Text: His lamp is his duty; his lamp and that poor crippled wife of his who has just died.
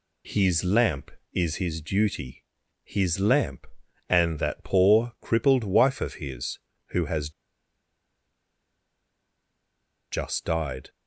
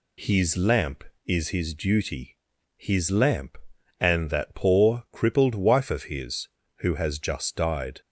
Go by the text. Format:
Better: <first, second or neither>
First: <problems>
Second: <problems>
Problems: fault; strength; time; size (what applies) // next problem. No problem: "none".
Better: second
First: pauses between "has" and "just"; strong; at 7.2 s; 2.8 s long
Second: none